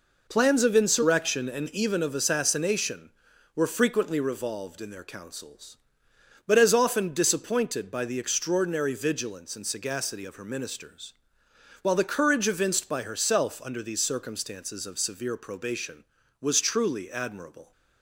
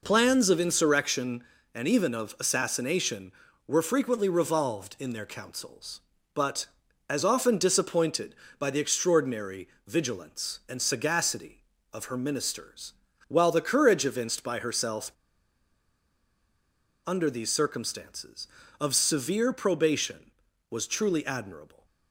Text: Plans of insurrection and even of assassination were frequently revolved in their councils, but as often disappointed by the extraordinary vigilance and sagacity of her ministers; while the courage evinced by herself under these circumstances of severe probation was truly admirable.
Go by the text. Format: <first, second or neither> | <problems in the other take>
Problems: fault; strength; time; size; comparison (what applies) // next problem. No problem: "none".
first | pauses between "extraordinary" and "vigilance"; slight; at 9.6 s; 0.22 s long // pauses between "herself" and "under"; strong; at 15.0 s; 1.9 s long